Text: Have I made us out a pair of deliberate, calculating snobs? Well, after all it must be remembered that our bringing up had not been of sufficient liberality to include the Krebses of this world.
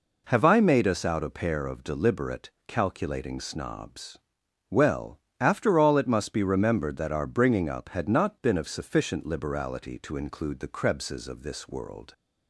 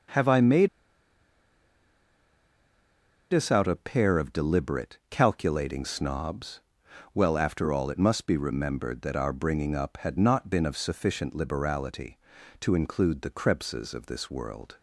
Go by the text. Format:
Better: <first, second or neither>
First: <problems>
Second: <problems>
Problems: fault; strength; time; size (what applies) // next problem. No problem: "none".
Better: first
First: none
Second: starts louder than the rest; until 3.7 s; 6 dB // pauses between "made" and "us"; strong; at 0.6 s; 2.6 s long